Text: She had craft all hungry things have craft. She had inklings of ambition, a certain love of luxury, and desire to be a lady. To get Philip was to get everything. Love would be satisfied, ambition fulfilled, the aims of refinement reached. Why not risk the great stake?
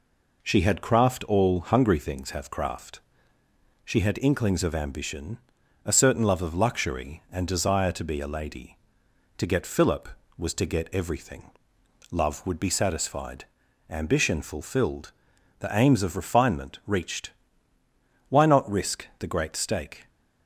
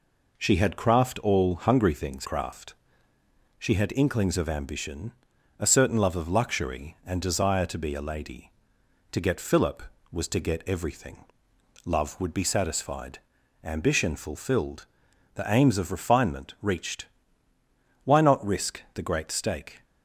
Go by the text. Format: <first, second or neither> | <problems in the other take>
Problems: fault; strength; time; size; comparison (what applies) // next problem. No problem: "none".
first | skips "have"; at 2.2 s